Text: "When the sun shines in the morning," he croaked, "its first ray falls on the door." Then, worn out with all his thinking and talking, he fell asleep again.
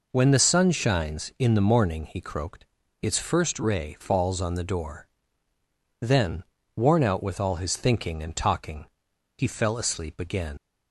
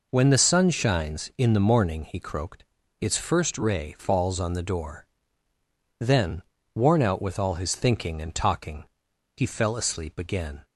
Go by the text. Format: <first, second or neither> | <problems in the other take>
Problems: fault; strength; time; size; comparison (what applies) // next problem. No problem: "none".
second | leaves "again" unfinished; at 10.5 s; 85 ms